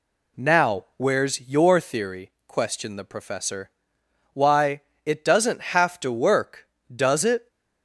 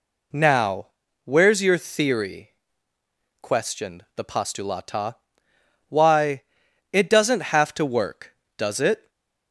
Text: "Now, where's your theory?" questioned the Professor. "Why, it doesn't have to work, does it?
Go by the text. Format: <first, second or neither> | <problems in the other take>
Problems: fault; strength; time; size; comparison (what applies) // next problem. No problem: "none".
first | says "Postulata" for "Professor"; at 4.2 s // stays silent after the last word; slight; from 8.9 s on; 0.6 s long